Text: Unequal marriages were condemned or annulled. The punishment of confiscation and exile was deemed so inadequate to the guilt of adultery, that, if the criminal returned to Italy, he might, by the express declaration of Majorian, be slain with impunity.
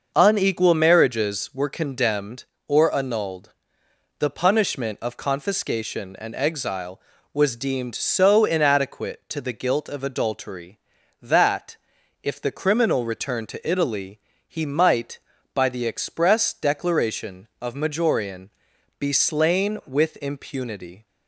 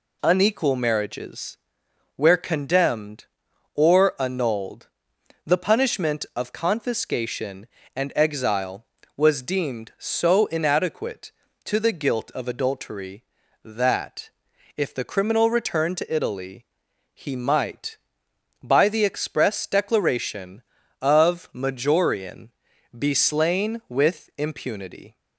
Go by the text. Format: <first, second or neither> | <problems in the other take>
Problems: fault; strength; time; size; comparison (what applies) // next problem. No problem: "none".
first | says "where" for "were"; at 2.1 s